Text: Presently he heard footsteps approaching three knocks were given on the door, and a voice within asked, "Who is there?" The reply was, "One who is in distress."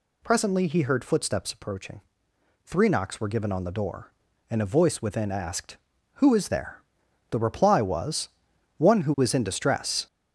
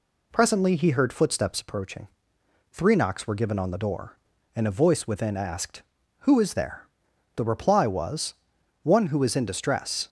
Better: second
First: gets louder; throughout; 6.5 dB // pauses between "approaching" and "three"; noticeable; at 2.0 s; 0.64 s long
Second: pauses between "approaching" and "three"; noticeable; at 2.0 s; 0.64 s long

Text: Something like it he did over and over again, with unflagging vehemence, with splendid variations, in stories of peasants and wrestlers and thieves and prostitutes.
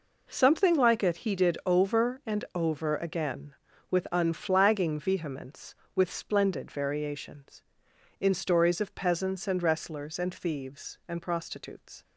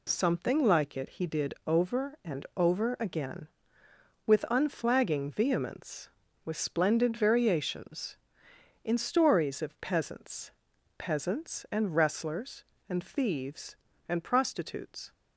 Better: first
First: none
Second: says "peasants" twice; at 10.9 s

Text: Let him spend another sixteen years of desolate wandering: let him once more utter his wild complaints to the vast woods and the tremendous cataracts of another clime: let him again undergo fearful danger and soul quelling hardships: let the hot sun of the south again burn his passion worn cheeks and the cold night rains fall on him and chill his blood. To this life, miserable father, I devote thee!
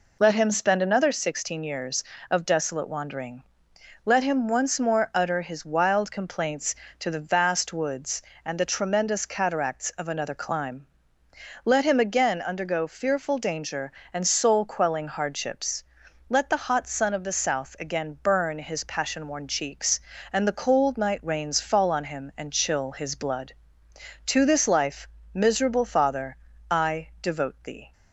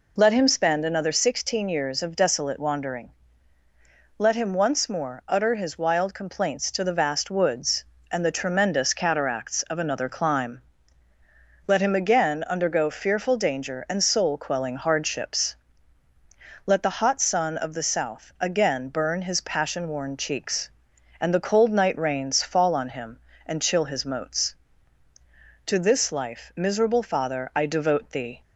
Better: first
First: none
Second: says "moats" for "blood"; at 24.0 s

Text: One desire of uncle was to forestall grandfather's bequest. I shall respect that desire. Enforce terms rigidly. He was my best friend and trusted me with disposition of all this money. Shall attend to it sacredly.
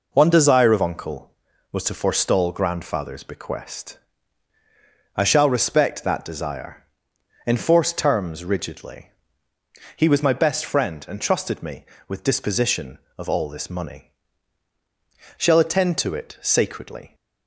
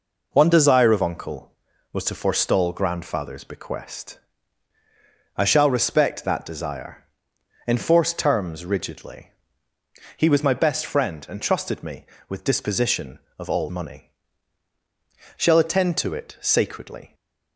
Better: first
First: none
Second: skips "this"; at 13.6 s

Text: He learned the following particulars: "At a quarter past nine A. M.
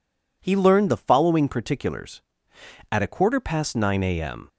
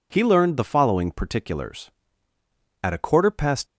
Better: first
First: none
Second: stops before "nine A M"; at 3.6 s

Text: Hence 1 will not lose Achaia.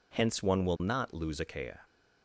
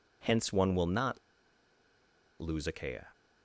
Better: first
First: none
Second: pauses between "not" and "lose"; at 1.1 s; 1.2 s long

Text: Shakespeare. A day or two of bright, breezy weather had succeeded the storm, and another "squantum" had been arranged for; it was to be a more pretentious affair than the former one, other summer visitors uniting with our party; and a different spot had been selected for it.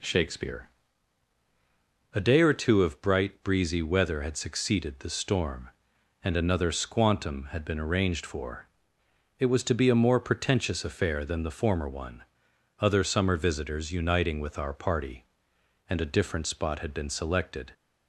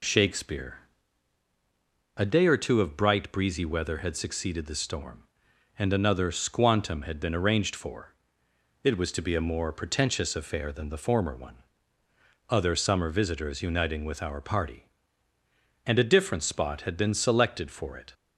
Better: second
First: stops before "for it"; at 17.7 s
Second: none

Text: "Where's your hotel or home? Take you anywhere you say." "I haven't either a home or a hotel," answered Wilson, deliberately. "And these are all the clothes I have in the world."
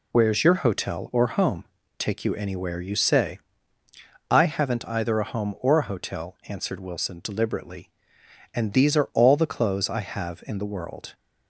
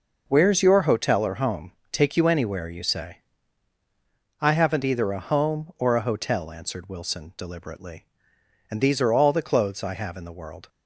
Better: neither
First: none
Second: none

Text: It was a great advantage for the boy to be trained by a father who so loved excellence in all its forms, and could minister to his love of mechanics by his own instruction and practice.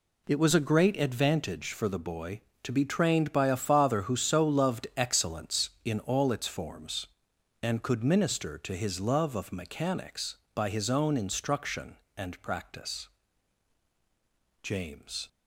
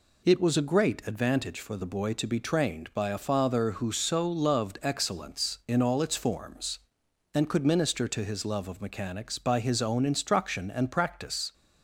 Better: second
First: goes on to say "James"; noticeable; from 14.6 s on; 0.66 s long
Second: none

